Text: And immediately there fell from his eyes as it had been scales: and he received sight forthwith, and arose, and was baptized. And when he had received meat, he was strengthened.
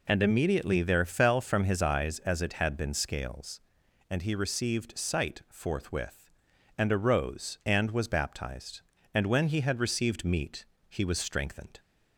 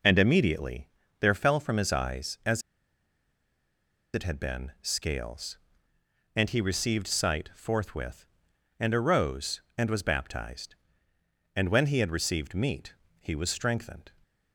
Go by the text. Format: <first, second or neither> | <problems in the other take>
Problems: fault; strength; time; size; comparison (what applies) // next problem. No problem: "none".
first | pauses between "immediately" and "there"; slight; at 0.8 s; 0.32 s long // pauses between "as" and "it"; strong; at 2.6 s; 1.5 s long